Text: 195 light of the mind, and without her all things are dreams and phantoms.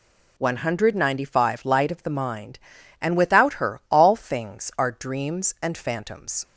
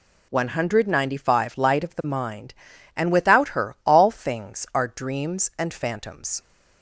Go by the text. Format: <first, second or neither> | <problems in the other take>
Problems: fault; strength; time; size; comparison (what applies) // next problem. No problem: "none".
neither | none